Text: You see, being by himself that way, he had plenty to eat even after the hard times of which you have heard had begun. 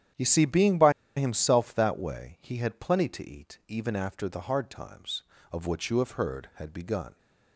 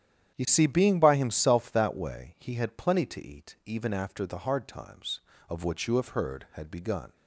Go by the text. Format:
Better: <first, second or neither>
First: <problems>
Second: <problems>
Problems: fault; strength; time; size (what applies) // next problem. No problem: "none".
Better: second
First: starts louder than the rest; strong; until 1.4 s; 10 dB // pauses between "by" and "himself"; slight; at 0.9 s; 0.25 s long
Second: starts louder than the rest; strong; until 1.3 s; 10 dB